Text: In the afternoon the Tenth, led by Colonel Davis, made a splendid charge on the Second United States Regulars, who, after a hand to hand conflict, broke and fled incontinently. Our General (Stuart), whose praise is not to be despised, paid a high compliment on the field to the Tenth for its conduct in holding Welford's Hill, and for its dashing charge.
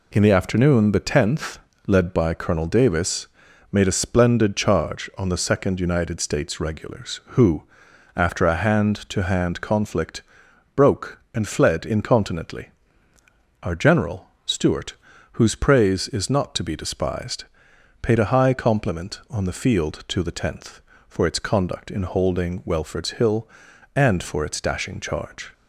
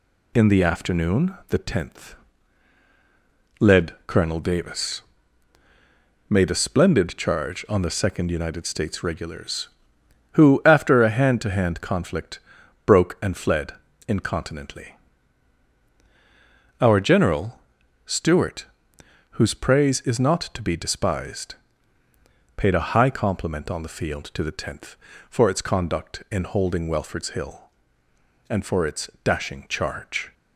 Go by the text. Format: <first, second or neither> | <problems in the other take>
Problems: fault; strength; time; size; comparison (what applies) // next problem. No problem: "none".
first | skips "by"; at 4.0 s // pauses between "fled" and "incontinently"; slight; at 13.7 s; 0.34 s long